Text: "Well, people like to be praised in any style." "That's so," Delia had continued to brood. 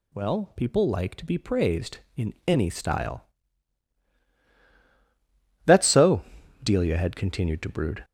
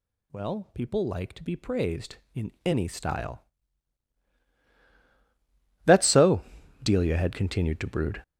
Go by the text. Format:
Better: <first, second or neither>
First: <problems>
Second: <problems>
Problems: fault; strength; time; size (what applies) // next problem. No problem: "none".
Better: first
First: none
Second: gets louder; strong; throughout; 9 dB